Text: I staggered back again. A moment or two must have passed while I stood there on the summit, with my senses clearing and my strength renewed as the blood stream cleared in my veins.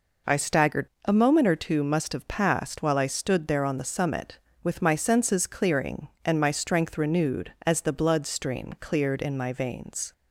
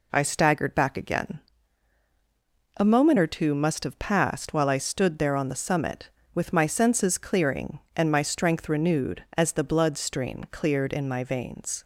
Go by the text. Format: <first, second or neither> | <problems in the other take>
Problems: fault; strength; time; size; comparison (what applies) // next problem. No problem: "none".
second | skips "back again"; at 0.9 s